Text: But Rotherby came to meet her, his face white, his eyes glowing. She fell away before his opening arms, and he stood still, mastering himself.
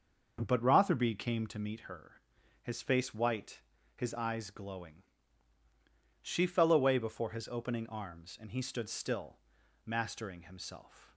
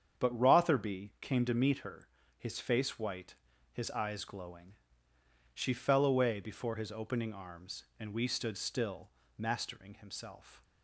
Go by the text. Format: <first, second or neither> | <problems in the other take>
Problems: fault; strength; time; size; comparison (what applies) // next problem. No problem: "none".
first | starts louder than the rest; strong; until 1.2 s; 8 dB; noticeable in the first // says "we" for "he"; at 8.1 s